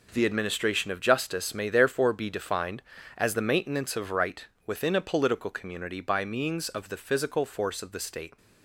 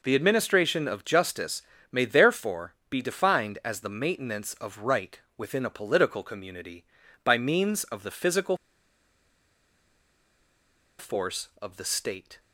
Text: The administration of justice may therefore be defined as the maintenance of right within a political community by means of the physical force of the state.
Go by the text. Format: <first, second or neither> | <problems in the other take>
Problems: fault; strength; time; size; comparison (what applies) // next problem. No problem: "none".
first | pauses between "justice" and "may"; slight; at 1.6 s; 0.30 s long // pauses between "right" and "within"; slight; at 5.1 s; 0.16 s long; slight in the first // pauses between "physical" and "force"; strong; at 8.5 s; 2.4 s long